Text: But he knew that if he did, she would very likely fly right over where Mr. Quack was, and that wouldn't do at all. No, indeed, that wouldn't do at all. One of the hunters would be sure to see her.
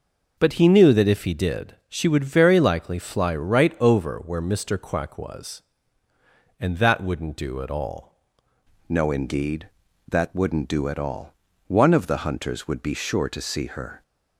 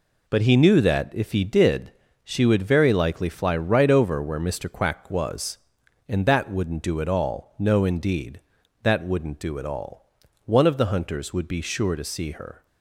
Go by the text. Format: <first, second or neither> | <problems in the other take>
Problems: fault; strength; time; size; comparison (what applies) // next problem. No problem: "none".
second | changes voice at "No"; from 8.8 s on; 5.2 s long